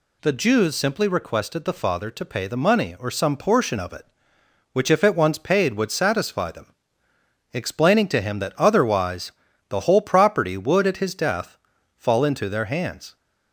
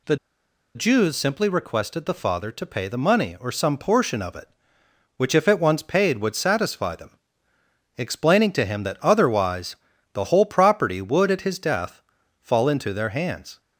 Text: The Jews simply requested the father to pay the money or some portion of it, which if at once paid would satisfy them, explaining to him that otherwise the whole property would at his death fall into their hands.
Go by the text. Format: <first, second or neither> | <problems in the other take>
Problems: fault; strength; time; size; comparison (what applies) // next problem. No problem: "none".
first | pauses between "The" and "Jews"; noticeable; at 0.1 s; 0.59 s long // pauses between "otherwise" and "the"; at 9.7 s; 0.38 s long; also in the first // pauses between "death" and "fall"; at 12.0 s; 0.38 s long; also in the first